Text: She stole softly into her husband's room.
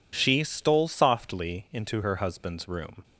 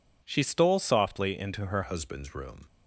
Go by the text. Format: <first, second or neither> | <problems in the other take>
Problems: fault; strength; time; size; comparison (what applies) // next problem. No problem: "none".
first | changes voice at "husband's"; from 1.8 s on; 0.8 s long